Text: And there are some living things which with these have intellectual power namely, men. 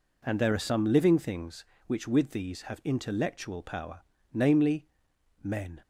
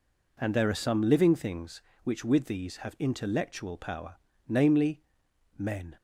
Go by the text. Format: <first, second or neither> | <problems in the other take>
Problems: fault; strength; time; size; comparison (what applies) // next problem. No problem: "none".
neither | pauses between "power" and "namely"; slight; the same in both